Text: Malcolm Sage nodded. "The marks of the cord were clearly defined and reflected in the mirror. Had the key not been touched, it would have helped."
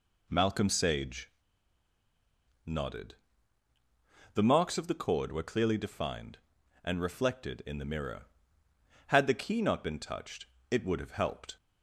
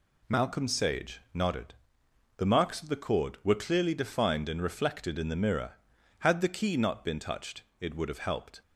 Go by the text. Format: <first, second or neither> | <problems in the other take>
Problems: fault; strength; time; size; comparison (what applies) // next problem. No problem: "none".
second | pauses between "Sage" and "nodded"; strong; at 1.3 s; 1.3 s long